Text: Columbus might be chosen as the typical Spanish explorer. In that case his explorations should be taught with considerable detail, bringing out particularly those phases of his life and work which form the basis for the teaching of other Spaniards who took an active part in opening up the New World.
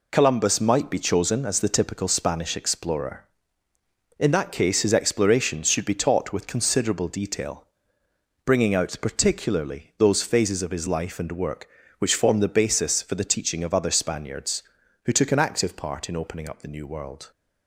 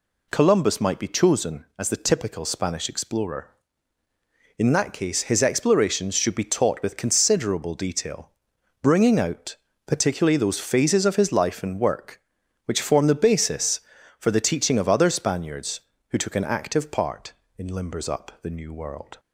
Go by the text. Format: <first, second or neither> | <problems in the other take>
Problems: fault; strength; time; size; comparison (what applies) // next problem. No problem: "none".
first | pauses between "out" and "particularly"; slight; at 9.5 s; 0.30 s long // says "limbers" for "opening"; at 17.7 s